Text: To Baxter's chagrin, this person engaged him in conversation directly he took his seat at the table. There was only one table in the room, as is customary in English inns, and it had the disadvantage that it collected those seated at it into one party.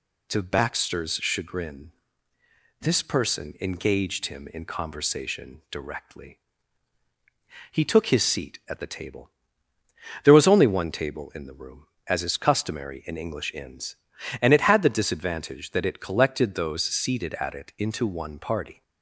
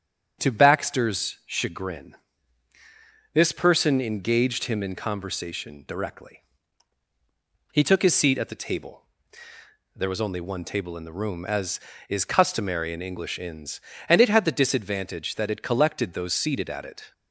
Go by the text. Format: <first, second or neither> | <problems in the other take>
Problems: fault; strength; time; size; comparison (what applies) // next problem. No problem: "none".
first | starts louder than the rest; strong; until 1.4 s; 8 dB // pauses between "directly" and "he"; strong; at 6.4 s; 1.3 s long; strong in the first // stops before "into one party"; at 17.1 s